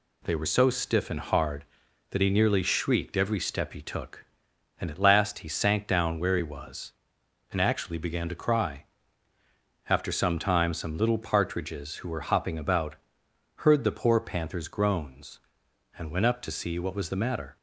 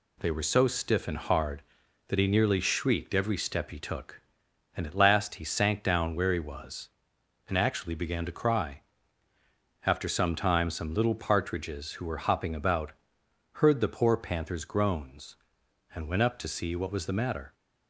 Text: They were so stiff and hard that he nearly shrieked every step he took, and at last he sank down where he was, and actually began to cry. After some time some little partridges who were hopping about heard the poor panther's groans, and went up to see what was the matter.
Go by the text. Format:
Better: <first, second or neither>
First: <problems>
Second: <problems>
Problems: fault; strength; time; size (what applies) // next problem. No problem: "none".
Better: neither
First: pauses between "about" and "heard"; noticeable; at 12.9 s; 0.62 s long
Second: pauses between "about" and "heard"; noticeable; at 12.9 s; 0.62 s long